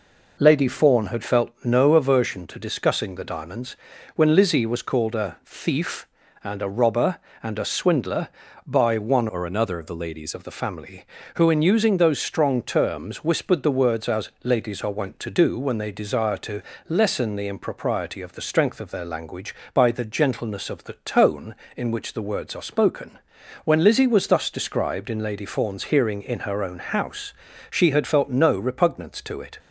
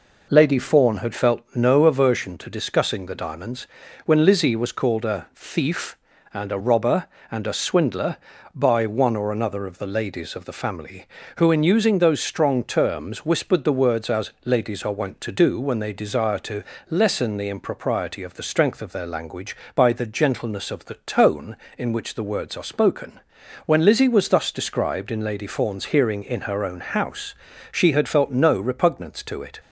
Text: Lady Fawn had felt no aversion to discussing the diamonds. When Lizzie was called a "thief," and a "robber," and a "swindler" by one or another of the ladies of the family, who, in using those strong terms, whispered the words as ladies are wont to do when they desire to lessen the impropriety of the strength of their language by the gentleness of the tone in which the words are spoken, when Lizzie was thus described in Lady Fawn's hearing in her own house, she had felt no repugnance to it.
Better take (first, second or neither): second